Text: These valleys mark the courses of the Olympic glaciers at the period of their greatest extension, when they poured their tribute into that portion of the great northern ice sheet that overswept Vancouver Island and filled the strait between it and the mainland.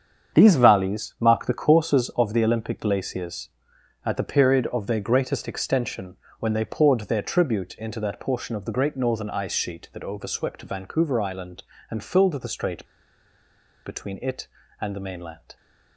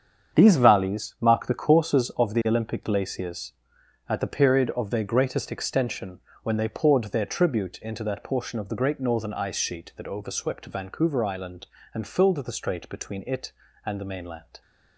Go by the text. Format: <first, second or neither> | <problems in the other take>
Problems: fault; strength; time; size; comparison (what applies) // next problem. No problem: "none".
second | starts louder than the rest; strong; until 1.4 s; 7.5 dB; strong in the second // pauses between "strait" and "between"; at 12.8 s; 1.0 s long